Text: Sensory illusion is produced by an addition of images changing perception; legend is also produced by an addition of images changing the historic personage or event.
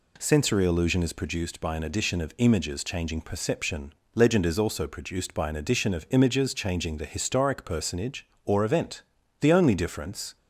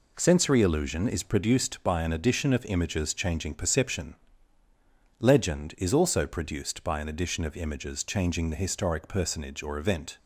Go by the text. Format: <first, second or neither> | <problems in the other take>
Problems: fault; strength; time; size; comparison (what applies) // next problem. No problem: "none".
second | goes on to say "The only difference"; noticeable; from 9.4 s on; 0.96 s long